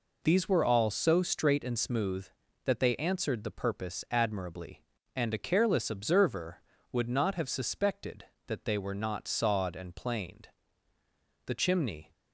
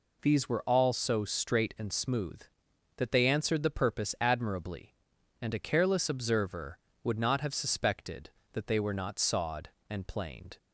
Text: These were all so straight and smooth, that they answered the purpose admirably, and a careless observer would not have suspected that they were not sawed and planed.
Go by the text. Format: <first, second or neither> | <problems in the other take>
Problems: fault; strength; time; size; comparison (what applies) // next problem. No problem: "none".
second | goes on to say "The chimney"; noticeable; from 11.4 s on; 0.66 s long